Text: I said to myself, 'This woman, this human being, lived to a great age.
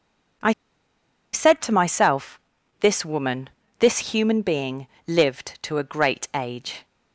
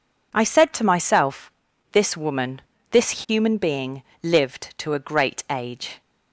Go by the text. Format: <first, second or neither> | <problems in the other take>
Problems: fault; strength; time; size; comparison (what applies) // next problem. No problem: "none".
second | pauses between "I" and "said"; noticeable; at 0.5 s; 0.80 s long